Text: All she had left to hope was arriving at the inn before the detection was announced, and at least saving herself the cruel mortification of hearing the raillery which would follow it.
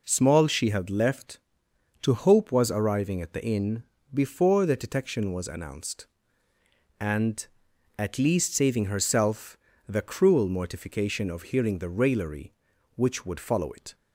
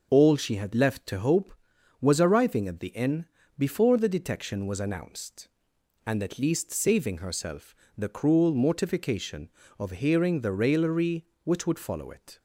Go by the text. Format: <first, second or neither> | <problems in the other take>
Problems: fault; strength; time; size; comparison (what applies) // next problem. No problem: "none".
second | says "Small" for "All"; at 0.0 s // pauses between "inn" and "before"; slight; at 3.8 s; 0.30 s long; slight in the second // pauses between "herself" and "the"; slight; at 9.5 s; 0.32 s long; slight in the second